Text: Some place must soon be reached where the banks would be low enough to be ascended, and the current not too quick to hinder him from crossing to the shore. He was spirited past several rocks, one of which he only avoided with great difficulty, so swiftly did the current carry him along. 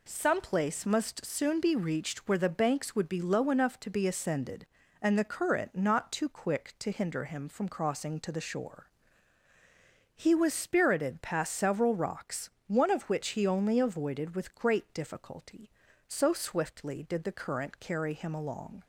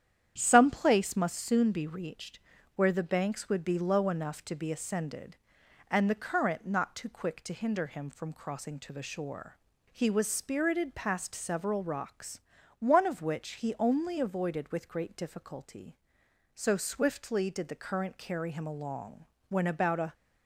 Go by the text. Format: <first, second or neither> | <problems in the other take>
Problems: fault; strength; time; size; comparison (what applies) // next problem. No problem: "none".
first | starts louder than the rest; strong; until 1.3 s; 9.5 dB // pauses between "reached" and "where"; slight; at 2.3 s; 0.36 s long // goes on to say "When about a"; noticeable; from 19.4 s on; 0.64 s long